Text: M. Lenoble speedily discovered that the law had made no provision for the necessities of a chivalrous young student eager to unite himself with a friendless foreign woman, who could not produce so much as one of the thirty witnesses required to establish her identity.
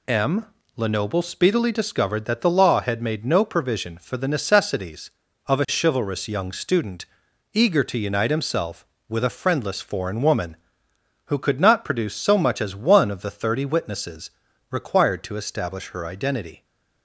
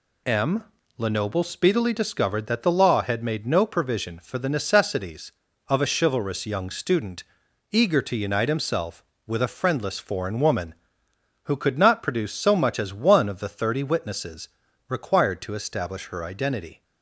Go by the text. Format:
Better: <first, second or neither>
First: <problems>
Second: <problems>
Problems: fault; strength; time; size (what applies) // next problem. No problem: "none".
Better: neither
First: pauses between "student" and "eager"; noticeable; at 7.0 s; 0.48 s long // pauses between "witnesses" and "required"; at 14.3 s; 0.40 s long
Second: pauses between "student" and "eager"; noticeable; at 7.2 s; 0.48 s long // pauses between "witnesses" and "required"; at 14.4 s; 0.40 s long